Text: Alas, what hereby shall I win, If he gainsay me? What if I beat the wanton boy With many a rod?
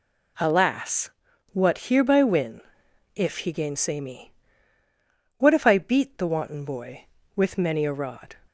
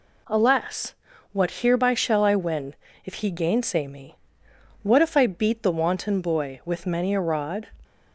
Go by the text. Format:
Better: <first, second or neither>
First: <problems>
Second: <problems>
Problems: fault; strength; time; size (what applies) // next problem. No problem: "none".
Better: second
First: skips "shall I"; at 2.2 s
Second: none